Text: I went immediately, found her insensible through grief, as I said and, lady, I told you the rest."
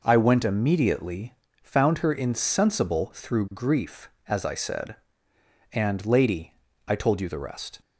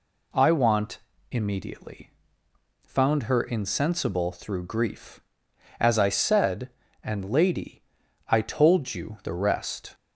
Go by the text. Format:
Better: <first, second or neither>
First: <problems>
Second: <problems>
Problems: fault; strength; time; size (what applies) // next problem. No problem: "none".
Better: first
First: none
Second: says "want" for "went"; at 0.5 s